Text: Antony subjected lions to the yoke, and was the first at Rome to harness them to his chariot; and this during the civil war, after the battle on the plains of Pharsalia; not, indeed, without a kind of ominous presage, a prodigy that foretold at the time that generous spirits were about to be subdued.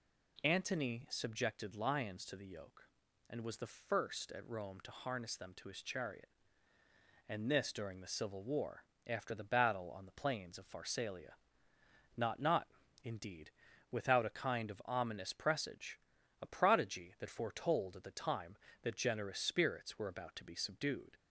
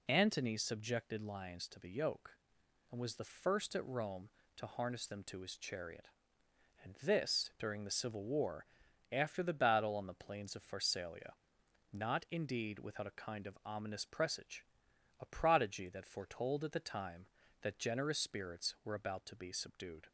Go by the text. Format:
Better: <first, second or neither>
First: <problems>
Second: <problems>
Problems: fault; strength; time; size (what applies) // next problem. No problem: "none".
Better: second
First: says "not" twice; at 12.3 s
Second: none